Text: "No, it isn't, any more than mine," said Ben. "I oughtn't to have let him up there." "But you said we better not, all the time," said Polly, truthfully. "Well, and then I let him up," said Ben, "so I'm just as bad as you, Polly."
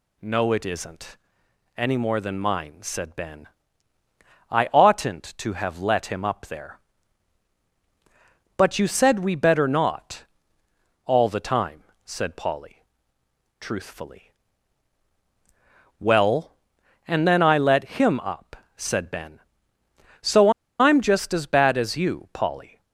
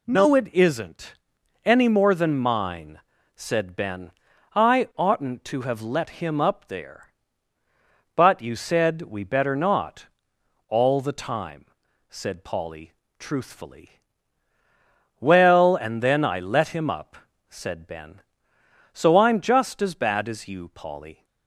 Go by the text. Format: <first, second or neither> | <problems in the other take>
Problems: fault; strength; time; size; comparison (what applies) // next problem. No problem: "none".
second | pauses between "so" and "I'm"; slight; at 20.5 s; 0.29 s long